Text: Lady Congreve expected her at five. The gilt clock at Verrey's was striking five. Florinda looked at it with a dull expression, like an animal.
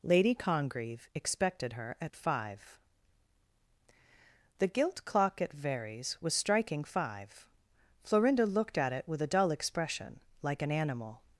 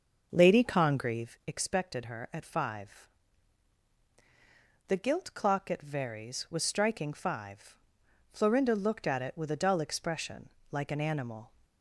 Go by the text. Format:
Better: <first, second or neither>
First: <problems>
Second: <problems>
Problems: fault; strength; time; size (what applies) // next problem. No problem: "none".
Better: first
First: none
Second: starts louder than the rest; noticeable; until 1.4 s; 6 dB